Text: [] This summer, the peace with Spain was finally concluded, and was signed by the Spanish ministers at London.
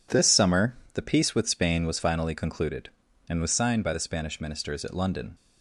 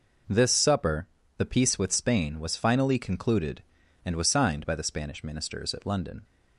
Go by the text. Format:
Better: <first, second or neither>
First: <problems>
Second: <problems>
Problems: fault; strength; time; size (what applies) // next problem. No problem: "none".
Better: first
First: none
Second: says "supper" for "summer"; at 0.4 s